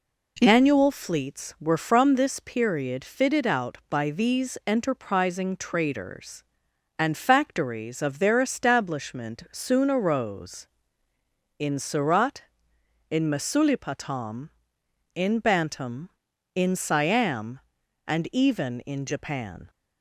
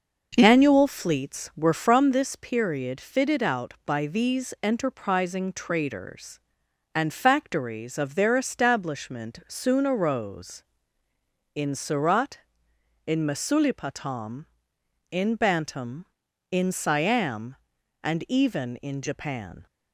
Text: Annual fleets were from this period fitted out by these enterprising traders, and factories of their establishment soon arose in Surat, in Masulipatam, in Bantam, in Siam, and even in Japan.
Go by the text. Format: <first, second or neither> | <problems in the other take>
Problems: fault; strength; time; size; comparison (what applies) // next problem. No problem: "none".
first | starts louder than the rest; noticeable; until 2.1 s; 6 dB